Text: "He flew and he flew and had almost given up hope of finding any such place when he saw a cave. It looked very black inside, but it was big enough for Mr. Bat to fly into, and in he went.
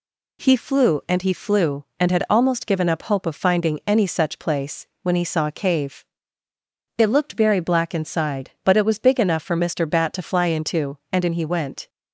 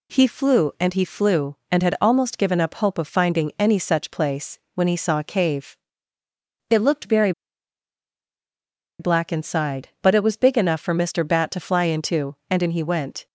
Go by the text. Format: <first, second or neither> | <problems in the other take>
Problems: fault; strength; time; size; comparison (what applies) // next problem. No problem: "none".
first | pauses between "place" and "when"; slight; at 4.5 s; 0.16 s long; slight in the first // pauses between "very" and "black"; strong; at 7.3 s; 1.6 s long